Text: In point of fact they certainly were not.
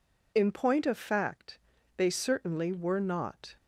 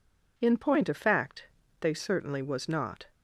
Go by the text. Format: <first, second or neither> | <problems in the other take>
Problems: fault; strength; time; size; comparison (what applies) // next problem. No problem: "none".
first | pauses between "fact" and "they"; slight; at 1.4 s; 0.34 s long; also in the first // says "was" for "were"; at 2.4 s